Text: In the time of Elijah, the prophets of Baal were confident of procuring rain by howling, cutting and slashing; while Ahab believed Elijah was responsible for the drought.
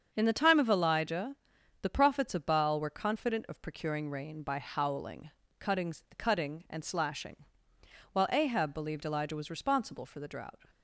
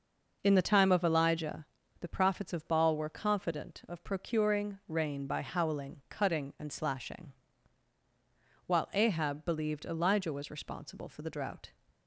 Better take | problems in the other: second | starts louder than the rest; until 1.1 s; 7 dB // says "cutting" twice; at 6.1 s

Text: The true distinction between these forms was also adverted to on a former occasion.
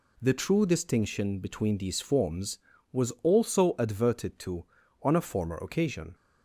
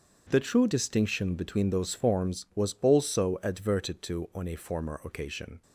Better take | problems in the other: first | starts louder than the rest; until 1.3 s; 7 dB // says "those" for "these"; at 1.6 s

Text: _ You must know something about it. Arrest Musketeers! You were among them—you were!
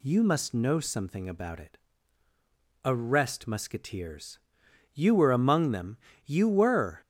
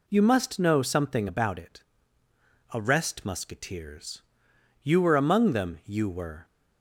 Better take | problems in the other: neither | none

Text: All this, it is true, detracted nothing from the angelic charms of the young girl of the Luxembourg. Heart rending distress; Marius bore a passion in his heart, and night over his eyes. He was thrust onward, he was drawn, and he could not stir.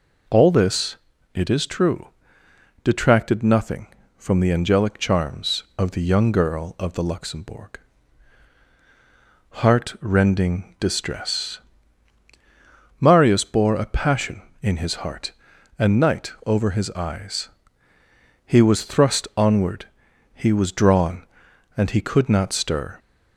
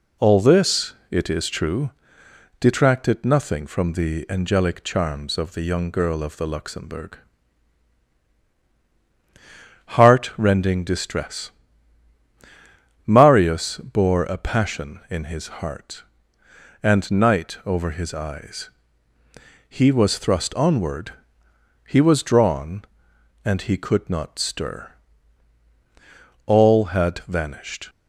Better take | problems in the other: first | goes on to say "All had vanished"; from 26.4 s on; 1.4 s long

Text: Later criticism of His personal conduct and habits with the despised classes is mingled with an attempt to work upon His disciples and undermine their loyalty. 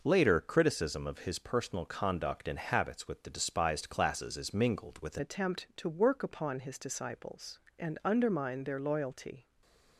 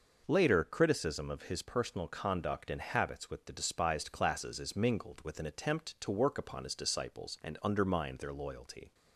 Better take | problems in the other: second | changes voice at "attempt"; from 5.1 s on; 4.3 s long // stays silent after the last word; slight; from 9.4 s on; 0.5 s long

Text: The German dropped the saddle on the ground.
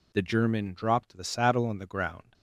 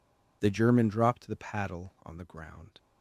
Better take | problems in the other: first | says "paddle" for "saddle"; at 1.3 s

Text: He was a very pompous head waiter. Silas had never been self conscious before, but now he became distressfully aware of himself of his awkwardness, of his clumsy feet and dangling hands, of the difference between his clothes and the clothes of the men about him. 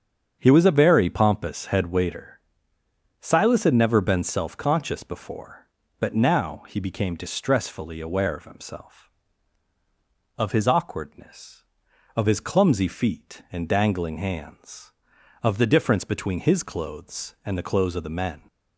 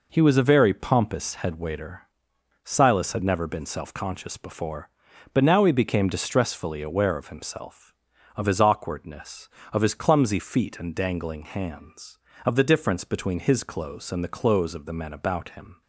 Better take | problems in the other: second | starts louder than the rest; strong; until 1.4 s; 7.5 dB // stops before "about him"; at 18.4 s

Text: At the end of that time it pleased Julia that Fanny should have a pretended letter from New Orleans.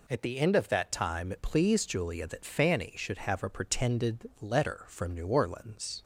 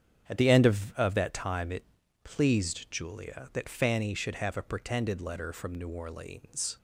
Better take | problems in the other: first | starts louder than the rest; strong; until 1.3 s; 8 dB // says "of" twice; at 0.9 s // pauses between "it" and "pleased"; at 1.8 s; 0.40 s long

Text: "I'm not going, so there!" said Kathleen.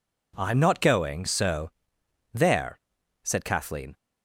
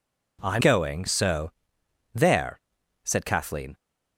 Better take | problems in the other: first | skips "not"; at 0.6 s // pauses between "so" and "there"; noticeable; at 1.5 s; 0.64 s long; noticeable in the first

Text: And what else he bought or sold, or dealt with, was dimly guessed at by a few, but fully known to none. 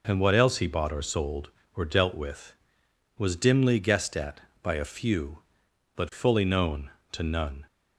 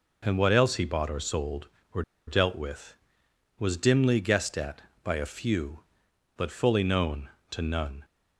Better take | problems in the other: first | pauses between "or" and "dealt"; slight; at 2.0 s; 0.25 s long

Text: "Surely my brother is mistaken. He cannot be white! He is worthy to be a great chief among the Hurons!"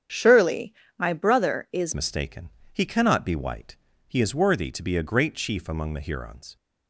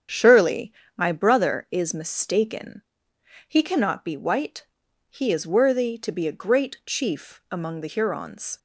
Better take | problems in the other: second | starts louder than the rest; strong; until 1.3 s; 8.5 dB; strong in the second // pauses between "Surely" and "my"; slight; at 0.7 s; 0.22 s long; slight in the second // changes voice at "mistaken"; from 1.9 s on; 4.6 s long

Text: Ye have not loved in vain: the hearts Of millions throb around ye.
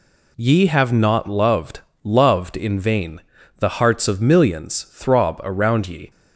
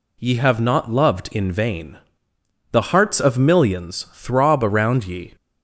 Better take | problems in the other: second | says "loved" twice; at 2.0 s

